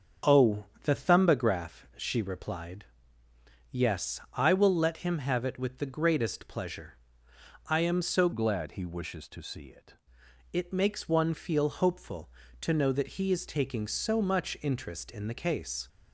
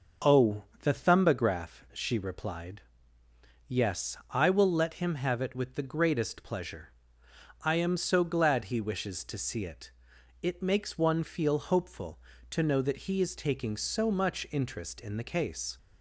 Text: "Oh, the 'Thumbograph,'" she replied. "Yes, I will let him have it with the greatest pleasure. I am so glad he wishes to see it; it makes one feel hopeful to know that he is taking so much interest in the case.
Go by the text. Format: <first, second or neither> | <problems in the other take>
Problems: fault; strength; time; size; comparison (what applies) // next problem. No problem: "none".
second | starts louder than the rest; strong; until 1.4 s; 7 dB; also in the second // changes voice from "glad" to "it"; from 8.3 to 9.9 s; 1.6 s long